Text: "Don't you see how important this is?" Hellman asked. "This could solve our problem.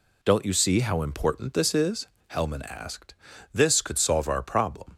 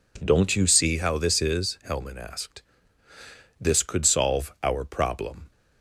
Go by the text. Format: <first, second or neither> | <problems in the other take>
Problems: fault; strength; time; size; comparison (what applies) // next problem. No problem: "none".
first | skips "important"; at 1.1 s